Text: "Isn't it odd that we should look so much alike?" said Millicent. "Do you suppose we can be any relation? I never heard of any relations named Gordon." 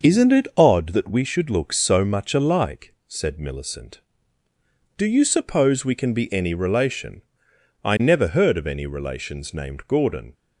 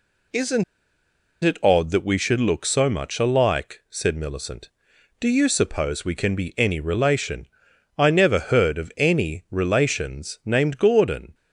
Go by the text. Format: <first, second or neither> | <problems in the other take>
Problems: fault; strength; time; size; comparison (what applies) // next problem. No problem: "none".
first | pauses between "Isn't" and "it"; noticeable; at 0.6 s; 0.80 s long